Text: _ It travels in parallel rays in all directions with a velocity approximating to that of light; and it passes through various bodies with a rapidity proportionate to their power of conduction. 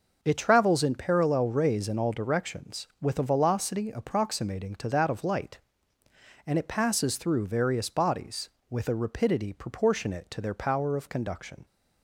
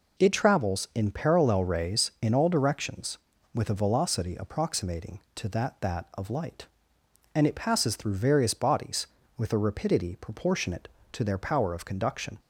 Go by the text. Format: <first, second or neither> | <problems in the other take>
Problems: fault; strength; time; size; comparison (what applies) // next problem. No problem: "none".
first | says "that" twice; at 5.8 s